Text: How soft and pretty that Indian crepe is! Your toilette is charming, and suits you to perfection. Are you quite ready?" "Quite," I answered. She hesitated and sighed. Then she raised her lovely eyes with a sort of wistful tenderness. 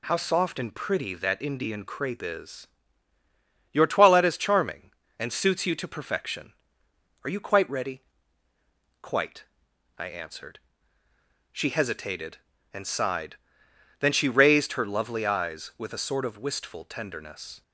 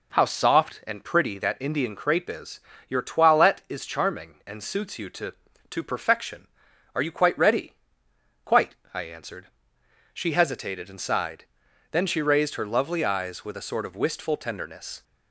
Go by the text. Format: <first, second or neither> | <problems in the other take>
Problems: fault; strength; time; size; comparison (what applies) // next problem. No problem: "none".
first | says "to" twice; at 5.6 s